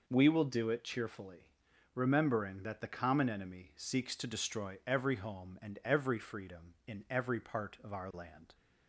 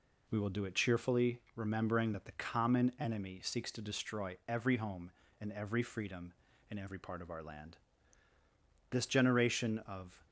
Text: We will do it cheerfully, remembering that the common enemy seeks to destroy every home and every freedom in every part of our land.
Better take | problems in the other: first | goes on to say "This generation of"; from 8.8 s on; 1.3 s long

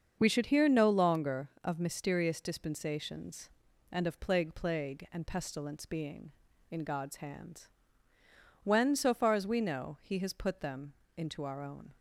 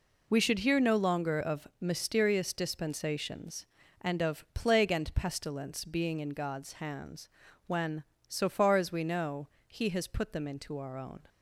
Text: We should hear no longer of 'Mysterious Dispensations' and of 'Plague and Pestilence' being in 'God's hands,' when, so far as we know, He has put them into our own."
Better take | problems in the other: second | starts louder than the rest; until 1.2 s; 6.5 dB // says "Plague" twice; at 4.5 s // pauses between "them" and "into"; slight; at 10.9 s; 0.22 s long

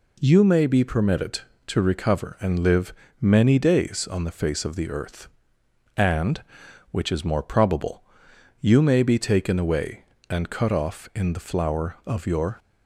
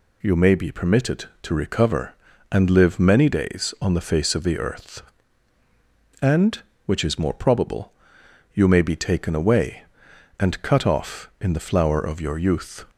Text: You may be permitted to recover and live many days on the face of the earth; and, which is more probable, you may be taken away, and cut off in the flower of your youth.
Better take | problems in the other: second | pauses between "live" and "many"; slight; at 2.9 s; 0.28 s long // stops before "youth"; at 12.5 s

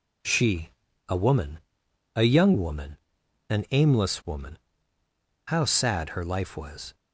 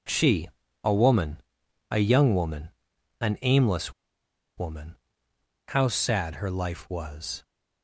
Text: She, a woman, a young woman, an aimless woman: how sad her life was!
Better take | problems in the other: first | pauses between "aimless" and "woman"; noticeable; at 3.9 s; 0.64 s long

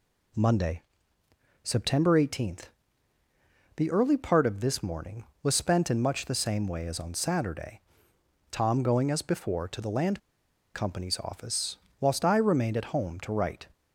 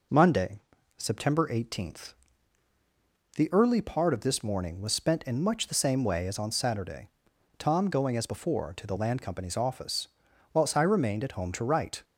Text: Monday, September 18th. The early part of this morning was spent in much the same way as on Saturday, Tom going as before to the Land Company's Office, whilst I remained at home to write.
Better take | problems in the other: second | pauses between "Land" and "Company's"; noticeable; at 10.1 s; 0.57 s long

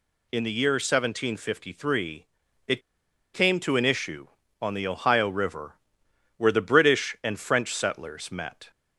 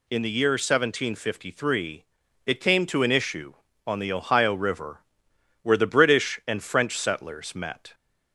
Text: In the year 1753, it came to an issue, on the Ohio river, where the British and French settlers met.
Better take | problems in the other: second | pauses between "it" and "came"; noticeable; at 2.8 s; 0.53 s long

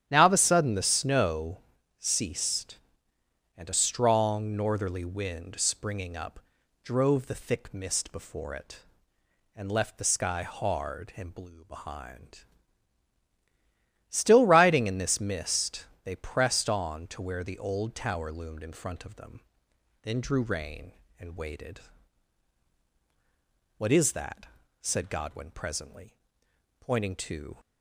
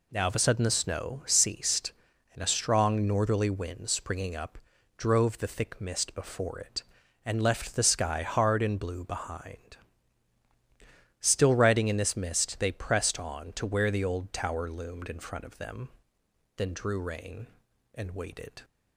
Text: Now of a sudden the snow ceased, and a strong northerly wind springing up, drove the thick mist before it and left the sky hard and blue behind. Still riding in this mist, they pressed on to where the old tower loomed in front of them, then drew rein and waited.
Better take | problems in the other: second | starts louder than the rest; strong; until 1.0 s; 10.5 dB // pauses between "snow" and "ceased"; at 1.5 s; 0.40 s long // goes on to say "What is that said Godwin presently pointing to"; strong; from 23.7 s on; 3.8 s long

